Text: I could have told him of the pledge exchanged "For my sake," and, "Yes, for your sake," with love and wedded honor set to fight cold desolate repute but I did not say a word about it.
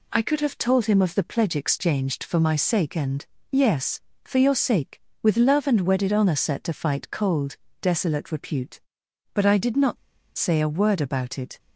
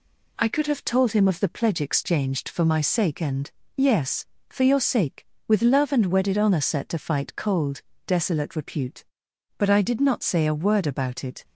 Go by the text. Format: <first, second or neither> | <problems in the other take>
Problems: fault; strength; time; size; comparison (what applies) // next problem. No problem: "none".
second | pauses between "cold" and "desolate"; slight; at 7.5 s; 0.24 s long; slight in the second // pauses between "not" and "say"; at 9.9 s; 0.41 s long